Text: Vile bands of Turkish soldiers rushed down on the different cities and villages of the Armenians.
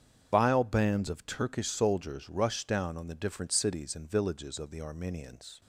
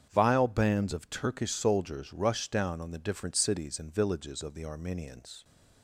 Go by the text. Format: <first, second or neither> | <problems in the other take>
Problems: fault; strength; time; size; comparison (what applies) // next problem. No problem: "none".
second | loses the start of "Vile"; at 0.3 s; 65 ms // starts louder than the rest; strong; until 1.3 s; 8 dB; strong in the second